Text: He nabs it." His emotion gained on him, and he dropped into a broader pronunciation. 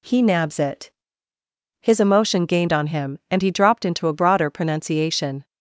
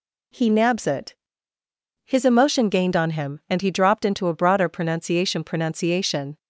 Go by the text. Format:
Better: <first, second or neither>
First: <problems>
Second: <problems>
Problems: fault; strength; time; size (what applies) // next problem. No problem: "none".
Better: first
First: none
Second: says "pronunciation" twice; at 5.4 s